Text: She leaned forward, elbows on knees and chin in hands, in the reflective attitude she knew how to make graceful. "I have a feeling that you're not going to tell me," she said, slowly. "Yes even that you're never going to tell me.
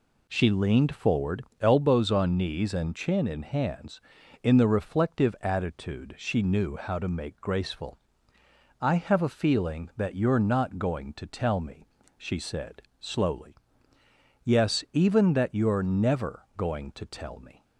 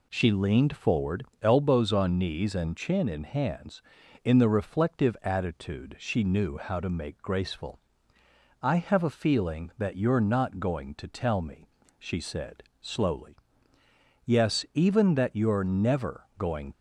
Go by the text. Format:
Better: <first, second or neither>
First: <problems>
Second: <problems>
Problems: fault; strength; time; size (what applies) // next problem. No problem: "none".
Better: first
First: none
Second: stops before "to tell me"; at 16.7 s